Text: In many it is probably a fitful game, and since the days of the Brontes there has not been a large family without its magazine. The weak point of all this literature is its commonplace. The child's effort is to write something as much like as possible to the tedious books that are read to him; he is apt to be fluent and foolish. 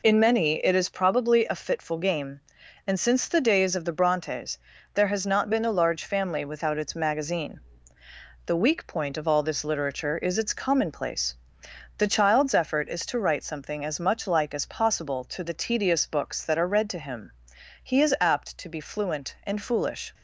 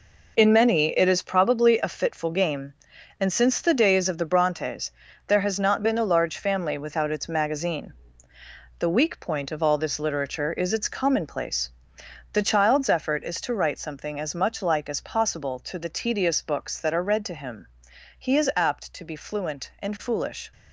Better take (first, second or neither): first